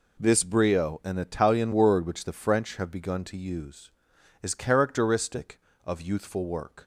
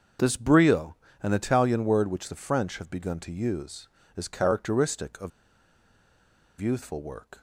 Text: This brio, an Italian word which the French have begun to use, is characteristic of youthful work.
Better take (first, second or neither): first